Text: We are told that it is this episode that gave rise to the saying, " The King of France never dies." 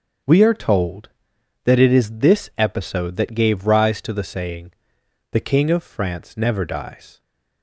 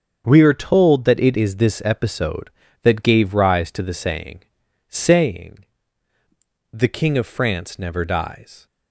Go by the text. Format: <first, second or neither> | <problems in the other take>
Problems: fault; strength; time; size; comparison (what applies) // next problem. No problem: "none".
first | starts louder than the rest; strong; until 1.2 s; 8 dB; also in the first // says "saying" twice; at 4.8 s